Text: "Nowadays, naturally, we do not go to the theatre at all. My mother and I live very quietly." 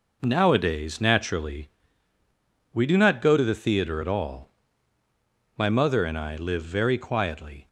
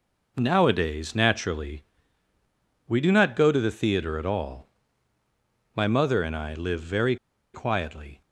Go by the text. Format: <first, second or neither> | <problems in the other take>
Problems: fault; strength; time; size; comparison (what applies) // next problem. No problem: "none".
first | pauses between "very" and "quietly"; at 7.1 s; 0.38 s long